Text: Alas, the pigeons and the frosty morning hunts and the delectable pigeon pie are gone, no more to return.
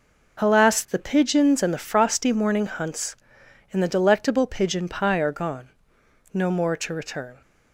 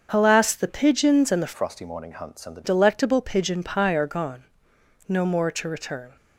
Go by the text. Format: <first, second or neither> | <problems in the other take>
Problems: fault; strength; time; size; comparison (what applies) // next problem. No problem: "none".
first | starts louder than the rest; until 1.1 s; 7 dB // changes voice from "frosty" to "the"; from 1.5 to 2.6 s; 1.1 s long